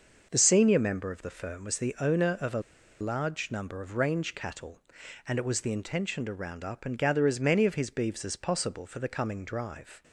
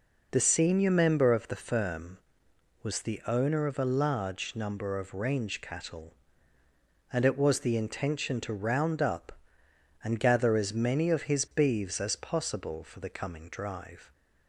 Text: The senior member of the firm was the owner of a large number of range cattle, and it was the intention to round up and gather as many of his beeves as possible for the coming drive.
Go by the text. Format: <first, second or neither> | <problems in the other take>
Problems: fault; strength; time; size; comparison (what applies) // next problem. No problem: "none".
second | starts louder than the rest; noticeable; until 1.3 s; 6 dB // pauses between "a" and "large"; at 2.6 s; 0.40 s long